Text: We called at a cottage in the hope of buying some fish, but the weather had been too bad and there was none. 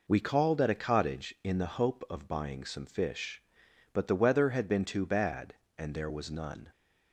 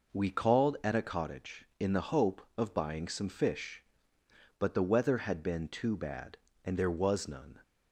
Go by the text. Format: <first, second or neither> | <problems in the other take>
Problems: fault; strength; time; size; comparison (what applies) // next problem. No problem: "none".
neither | none